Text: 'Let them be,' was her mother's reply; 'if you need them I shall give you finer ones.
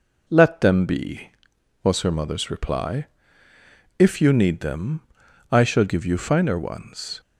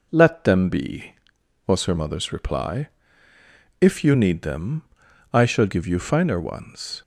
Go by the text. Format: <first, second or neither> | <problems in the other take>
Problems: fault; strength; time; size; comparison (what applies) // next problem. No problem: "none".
neither | pauses between "them" and "I"; noticeable; the same in both